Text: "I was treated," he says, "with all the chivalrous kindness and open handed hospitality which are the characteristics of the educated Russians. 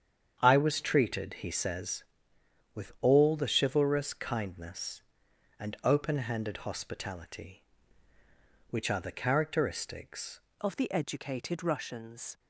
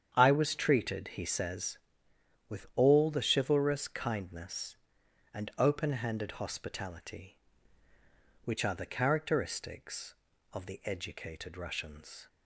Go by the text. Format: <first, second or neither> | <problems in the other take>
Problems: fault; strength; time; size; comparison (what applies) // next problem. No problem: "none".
second | starts louder than the rest; strong; until 1.4 s; 8 dB; strong in the second // changes voice at "of"; from 10.6 s on; 1.7 s long